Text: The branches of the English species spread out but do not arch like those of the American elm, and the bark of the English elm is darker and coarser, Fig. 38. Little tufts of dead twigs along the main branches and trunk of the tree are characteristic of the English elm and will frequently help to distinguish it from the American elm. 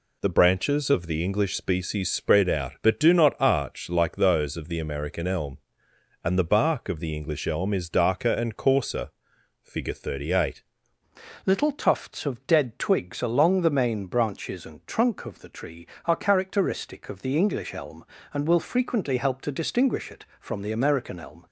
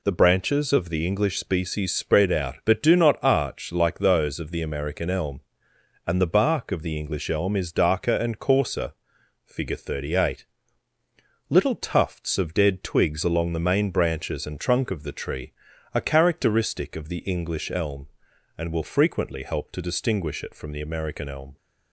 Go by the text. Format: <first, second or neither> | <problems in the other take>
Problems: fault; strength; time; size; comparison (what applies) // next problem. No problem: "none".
second | changes voice at "Little"; from 11.4 s on; 10.0 s long